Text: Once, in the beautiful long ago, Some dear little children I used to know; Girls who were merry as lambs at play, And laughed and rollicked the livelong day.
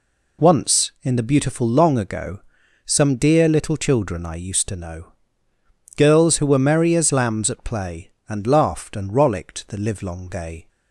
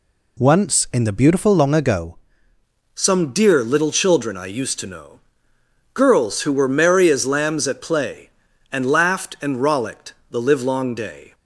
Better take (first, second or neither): first